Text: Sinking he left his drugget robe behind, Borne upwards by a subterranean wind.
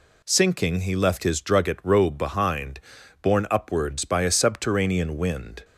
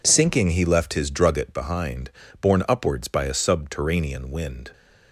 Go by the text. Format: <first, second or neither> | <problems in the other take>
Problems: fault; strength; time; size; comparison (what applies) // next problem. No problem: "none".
first | skips "robe"; at 1.5 s